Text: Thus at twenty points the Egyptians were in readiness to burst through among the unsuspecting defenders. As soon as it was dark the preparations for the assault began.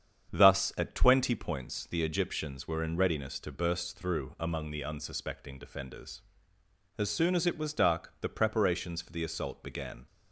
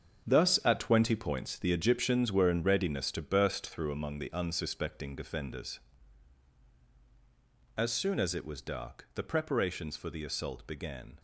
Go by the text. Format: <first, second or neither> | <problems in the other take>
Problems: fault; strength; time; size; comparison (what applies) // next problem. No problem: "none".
first | gets quieter; strong; throughout; 10.5 dB // starts louder than the rest; until 1.3 s; 7 dB; strong in the first